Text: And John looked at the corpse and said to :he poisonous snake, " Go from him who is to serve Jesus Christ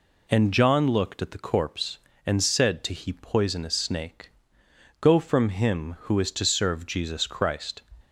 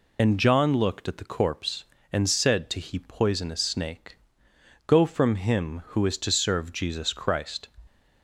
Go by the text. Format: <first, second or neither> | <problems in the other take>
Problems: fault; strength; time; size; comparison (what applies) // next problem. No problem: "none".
first | loses the start of "And"; at 0.1 s; 40 ms